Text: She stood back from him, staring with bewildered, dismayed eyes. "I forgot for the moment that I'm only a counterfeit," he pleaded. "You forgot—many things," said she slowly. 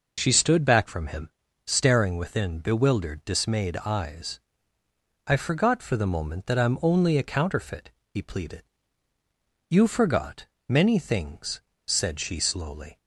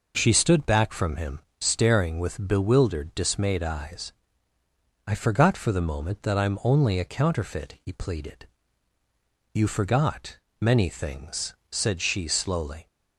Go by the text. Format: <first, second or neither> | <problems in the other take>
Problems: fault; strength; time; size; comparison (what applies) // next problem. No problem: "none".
second | says "within" for "with"; at 2.1 s